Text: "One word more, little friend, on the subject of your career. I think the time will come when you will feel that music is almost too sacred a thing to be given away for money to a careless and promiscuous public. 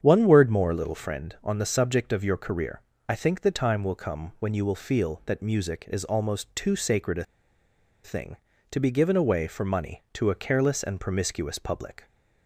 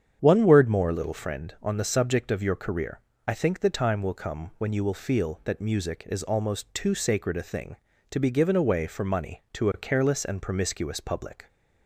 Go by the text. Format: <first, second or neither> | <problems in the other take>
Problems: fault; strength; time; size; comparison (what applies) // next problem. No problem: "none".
second | starts louder than the rest; strong; until 1.0 s; 8 dB; strong in the second // pauses between "a" and "thing"; noticeable; at 7.2 s; 0.79 s long